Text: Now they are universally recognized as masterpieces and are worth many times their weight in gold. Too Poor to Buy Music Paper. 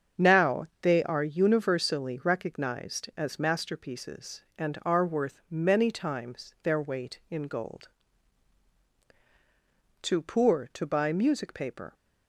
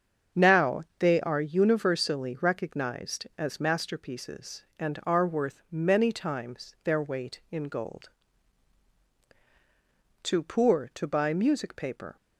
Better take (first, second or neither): neither